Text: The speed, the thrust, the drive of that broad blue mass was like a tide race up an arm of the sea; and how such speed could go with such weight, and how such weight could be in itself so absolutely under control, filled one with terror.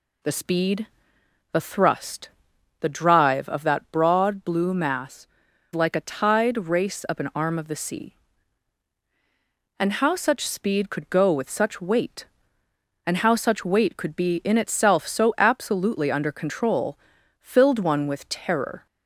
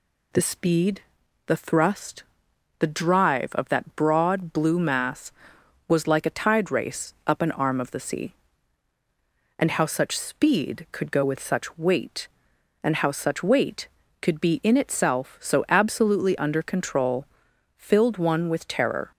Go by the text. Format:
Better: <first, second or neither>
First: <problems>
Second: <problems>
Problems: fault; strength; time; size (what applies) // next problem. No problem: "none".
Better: second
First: skips "was"; at 5.4 s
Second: none